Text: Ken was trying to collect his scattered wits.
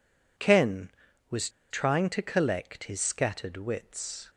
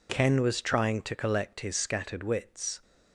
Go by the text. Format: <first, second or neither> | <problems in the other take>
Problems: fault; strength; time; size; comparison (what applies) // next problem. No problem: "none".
second | pauses between "was" and "trying"; slight; at 1.4 s; 0.21 s long